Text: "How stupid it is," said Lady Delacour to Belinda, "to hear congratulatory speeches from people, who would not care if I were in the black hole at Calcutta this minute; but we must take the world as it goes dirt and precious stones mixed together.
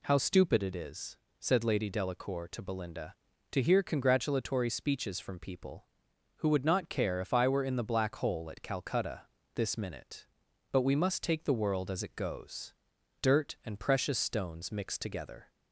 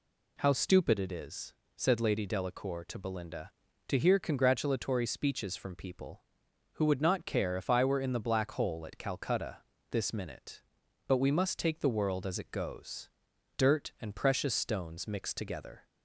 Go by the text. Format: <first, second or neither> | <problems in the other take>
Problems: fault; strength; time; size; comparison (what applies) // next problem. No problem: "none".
neither | pauses between "Calcutta" and "this"; slight; the same in both // pauses between "goes" and "dirt"; noticeable; the same in both